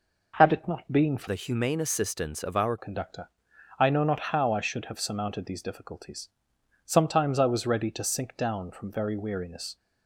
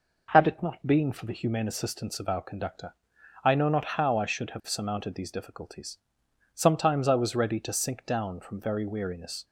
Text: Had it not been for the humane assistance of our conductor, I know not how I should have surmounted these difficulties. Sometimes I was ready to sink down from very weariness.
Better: second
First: changes voice from "the" to "our"; from 1.2 to 2.7 s; 1.5 s long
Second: none

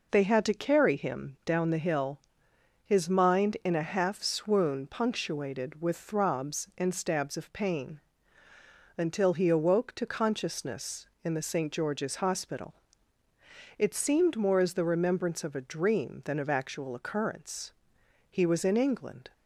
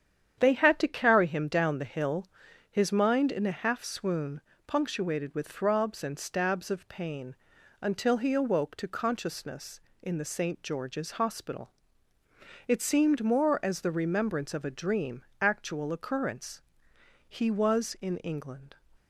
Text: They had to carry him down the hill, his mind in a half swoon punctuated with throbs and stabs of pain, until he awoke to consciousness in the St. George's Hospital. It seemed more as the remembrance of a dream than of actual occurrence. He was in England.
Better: first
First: none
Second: starts louder than the rest; strong; until 1.4 s; 9 dB // pauses between "swoon" and "punctuated"; slight; at 4.3 s; 0.26 s long // skips "than of"; at 15.3 s

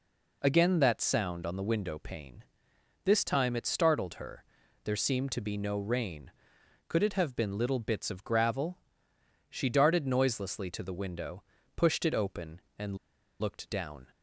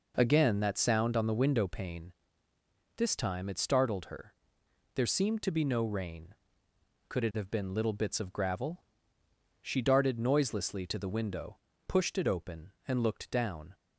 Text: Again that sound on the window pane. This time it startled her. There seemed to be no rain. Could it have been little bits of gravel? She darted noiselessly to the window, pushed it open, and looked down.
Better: second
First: pauses between "and" and "looked"; at 12.9 s; 0.45 s long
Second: none

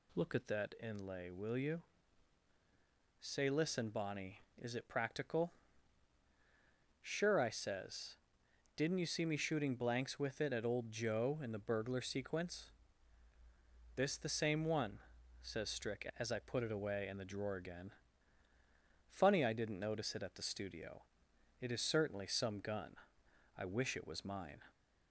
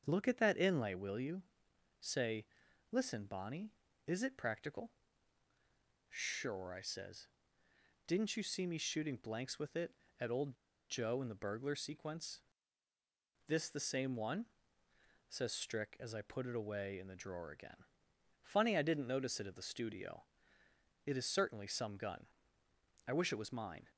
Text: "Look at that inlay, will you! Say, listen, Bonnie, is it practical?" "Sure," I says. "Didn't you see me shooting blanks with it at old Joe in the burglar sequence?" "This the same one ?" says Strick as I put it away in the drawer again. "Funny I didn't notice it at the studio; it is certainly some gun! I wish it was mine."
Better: first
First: none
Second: starts louder than the rest; until 1.0 s; 7 dB // pauses between "old" and "Joe"; slight; at 10.5 s; 0.35 s long

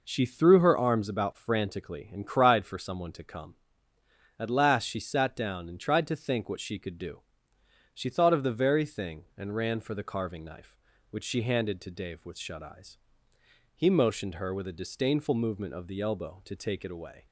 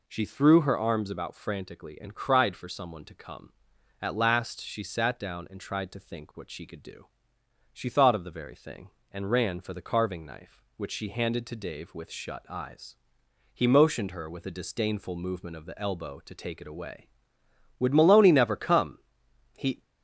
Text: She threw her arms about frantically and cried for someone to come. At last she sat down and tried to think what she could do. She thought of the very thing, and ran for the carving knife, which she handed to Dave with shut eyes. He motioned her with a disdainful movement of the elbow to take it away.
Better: first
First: none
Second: goes on to say "Would Maloney never come He"; strong; from 17.7 s on; 2.0 s long

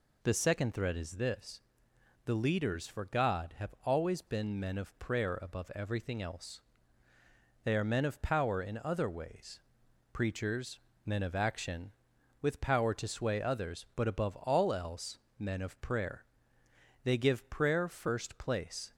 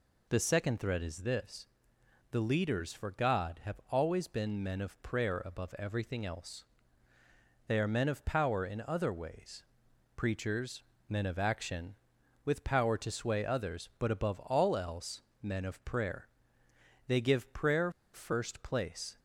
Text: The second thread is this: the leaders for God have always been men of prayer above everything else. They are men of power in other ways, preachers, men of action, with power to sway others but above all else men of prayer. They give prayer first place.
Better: first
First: pauses between "else" and "men"; slight; at 15.1 s; 0.20 s long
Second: pauses between "else" and "men"; slight; at 15.2 s; 0.20 s long // pauses between "prayer" and "first"; slight; at 17.8 s; 0.24 s long

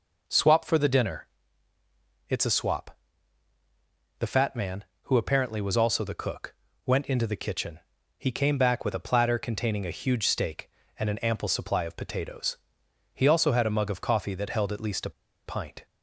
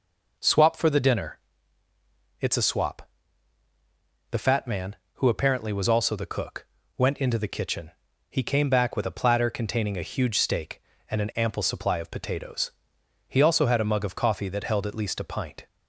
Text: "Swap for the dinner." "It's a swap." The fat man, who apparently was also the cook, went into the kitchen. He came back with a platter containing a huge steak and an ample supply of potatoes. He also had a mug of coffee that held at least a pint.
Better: second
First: pauses between "a" and "pint"; slight; at 15.1 s; 0.35 s long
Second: none

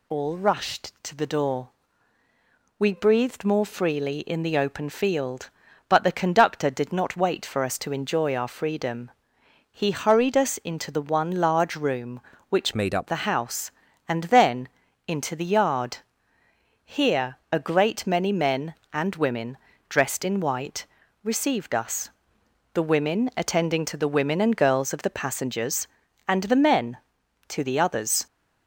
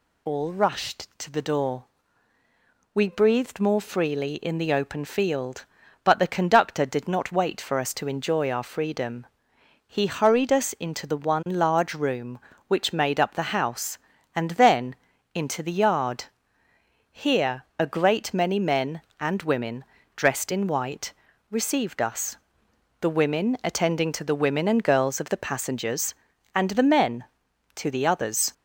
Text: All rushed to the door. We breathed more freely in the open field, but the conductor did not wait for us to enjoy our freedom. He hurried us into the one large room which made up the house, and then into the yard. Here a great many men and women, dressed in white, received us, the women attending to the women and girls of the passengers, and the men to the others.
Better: second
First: changes voice from "made" to "up"; from 12.7 to 13.0 s; 0.3 s long // pauses between "then" and "into"; at 14.6 s; 0.40 s long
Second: pauses between "then" and "into"; at 14.9 s; 0.40 s long

